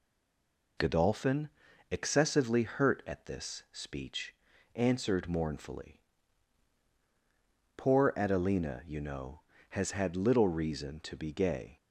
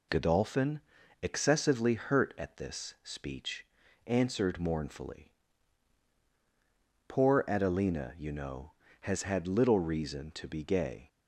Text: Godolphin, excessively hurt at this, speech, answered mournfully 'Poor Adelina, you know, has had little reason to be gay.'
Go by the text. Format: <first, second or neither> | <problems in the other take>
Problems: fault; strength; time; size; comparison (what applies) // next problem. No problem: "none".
second | stays silent before the first word; slight; until 0.7 s; 0.7 s long // pauses between "mournfully" and "Poor"; strong; at 5.9 s; 1.7 s long; strong in the second